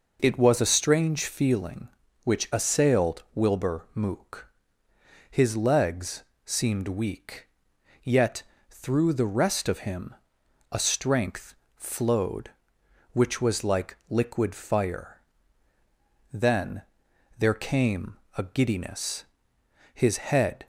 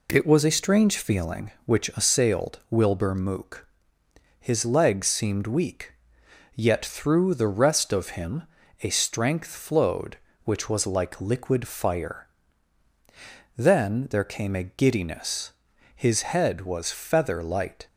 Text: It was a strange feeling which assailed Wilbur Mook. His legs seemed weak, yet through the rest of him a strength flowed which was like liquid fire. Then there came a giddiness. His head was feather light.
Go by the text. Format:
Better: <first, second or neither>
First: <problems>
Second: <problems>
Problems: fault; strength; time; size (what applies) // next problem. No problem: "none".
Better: second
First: pauses between "legs" and "seemed"; slight; at 6.2 s; 0.20 s long // pauses between "yet" and "through"; slight; at 8.4 s; 0.26 s long // pauses between "him" and "a"; noticeable; at 10.1 s; 0.56 s long // pauses between "strength" and "flowed"; slight; at 11.5 s; 0.20 s long // pauses between "Then" and "there"; noticeable; at 16.8 s; 0.56 s long // pauses between "came" and "a"; slight; at 18.1 s; 0.20 s long // stops before "was feather light"; at 20.6 s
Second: pauses between "him" and "a"; at 8.4 s; 0.40 s long